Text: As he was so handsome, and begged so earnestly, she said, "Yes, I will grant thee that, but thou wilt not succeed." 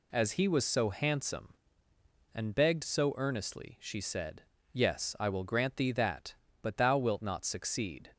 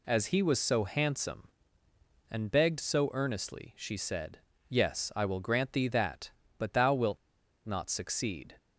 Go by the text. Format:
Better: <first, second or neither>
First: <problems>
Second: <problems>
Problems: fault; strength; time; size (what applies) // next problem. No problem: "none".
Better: first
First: none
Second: pauses between "wilt" and "not"; noticeable; at 7.1 s; 0.49 s long